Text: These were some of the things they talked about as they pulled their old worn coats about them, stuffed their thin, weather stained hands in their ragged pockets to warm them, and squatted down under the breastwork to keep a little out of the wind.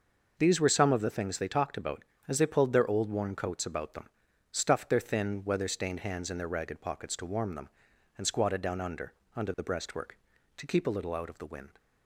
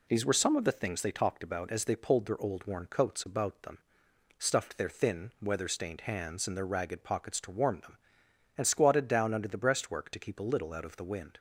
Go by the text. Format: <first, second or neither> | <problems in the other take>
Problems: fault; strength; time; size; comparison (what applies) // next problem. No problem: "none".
second | says "under" twice; at 9.3 s